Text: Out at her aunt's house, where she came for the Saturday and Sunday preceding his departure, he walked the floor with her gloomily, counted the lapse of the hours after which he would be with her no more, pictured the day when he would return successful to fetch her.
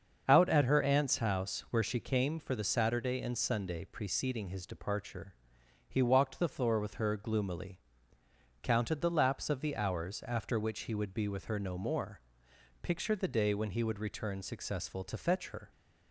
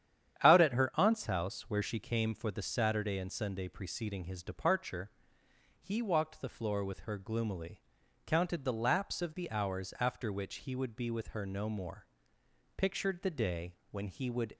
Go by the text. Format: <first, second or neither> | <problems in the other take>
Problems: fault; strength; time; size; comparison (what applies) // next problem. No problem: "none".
first | starts louder than the rest; strong; until 1.4 s; 9.5 dB; also in the first // pauses between "day" and "when"; slight; at 13.7 s; 0.18 s long // stops before "return successful to fetch her"; at 14.5 s